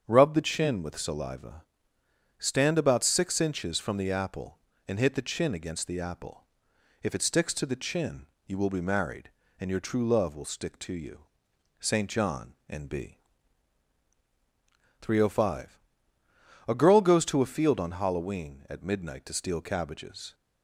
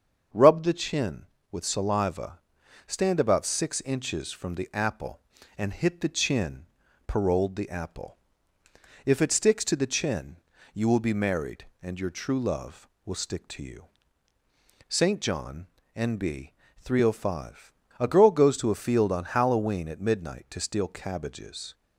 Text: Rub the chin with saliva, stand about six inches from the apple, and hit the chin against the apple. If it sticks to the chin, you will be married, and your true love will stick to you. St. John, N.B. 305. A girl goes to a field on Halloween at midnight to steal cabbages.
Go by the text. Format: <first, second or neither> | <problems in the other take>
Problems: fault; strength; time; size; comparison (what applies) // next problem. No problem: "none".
first | starts louder than the rest; until 1.5 s; 7 dB; strong in the first // says "paroled" for "against"; at 7.0 s